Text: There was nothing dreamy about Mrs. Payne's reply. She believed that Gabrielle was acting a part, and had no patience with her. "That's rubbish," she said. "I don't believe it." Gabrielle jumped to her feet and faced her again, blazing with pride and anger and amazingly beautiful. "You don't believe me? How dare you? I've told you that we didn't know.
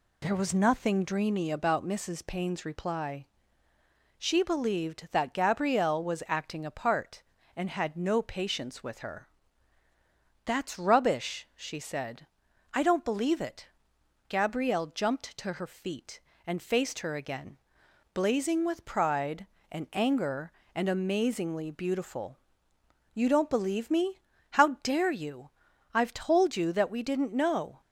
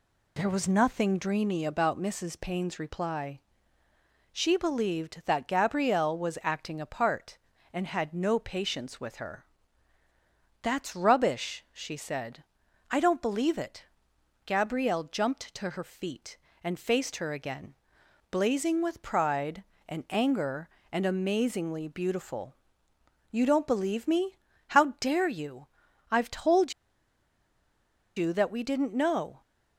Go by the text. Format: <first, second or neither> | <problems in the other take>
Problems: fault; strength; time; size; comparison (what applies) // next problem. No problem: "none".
first | pauses between "told" and "you"; strong; at 26.7 s; 1.4 s long